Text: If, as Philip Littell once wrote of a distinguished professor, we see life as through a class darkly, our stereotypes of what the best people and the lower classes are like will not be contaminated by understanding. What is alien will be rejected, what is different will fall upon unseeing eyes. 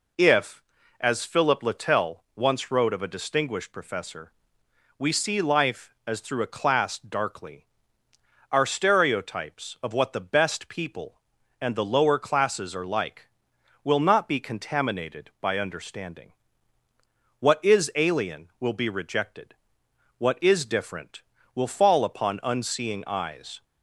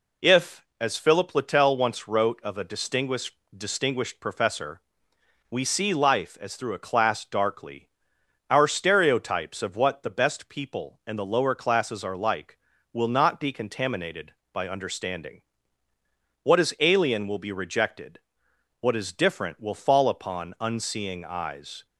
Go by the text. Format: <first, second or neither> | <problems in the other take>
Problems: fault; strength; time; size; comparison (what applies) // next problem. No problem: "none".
first | says "distinguished" twice; at 3.5 s